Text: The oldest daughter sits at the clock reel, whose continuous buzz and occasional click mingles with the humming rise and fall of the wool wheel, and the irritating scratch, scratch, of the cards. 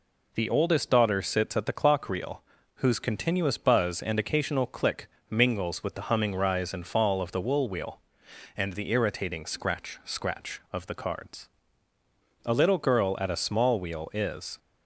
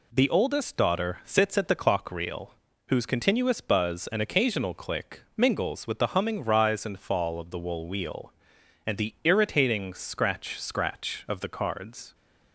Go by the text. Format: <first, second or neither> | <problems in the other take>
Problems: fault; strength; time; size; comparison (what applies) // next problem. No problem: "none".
second | pauses between "click" and "mingles"; slight; at 5.0 s; 0.22 s long // goes on to say "A little girl at a small wheel is"; strong; from 12.4 s on; 2.1 s long